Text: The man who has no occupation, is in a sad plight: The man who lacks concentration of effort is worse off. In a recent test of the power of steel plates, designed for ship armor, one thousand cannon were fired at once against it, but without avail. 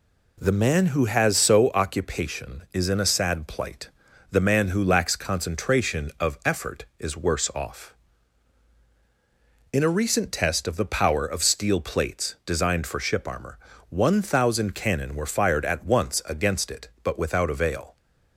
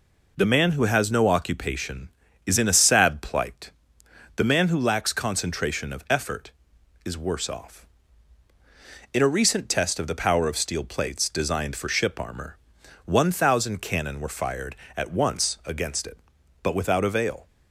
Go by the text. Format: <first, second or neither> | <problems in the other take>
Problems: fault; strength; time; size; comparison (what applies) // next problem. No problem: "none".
second | says "so" for "no"; at 1.3 s